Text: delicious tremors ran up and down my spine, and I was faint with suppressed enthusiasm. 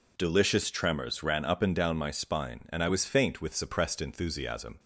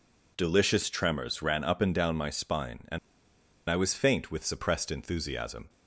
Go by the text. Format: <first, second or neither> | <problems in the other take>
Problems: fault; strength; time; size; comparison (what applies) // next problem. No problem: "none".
first | pauses between "and" and "I"; noticeable; at 2.9 s; 0.70 s long